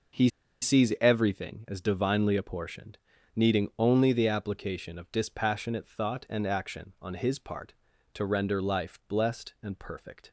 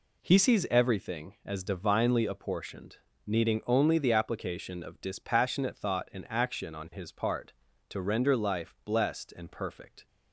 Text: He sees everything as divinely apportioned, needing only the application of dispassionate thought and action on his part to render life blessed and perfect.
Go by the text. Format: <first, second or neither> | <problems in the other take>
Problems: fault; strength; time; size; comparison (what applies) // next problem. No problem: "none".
second | pauses between "He" and "sees"; slight; at 0.2 s; 0.33 s long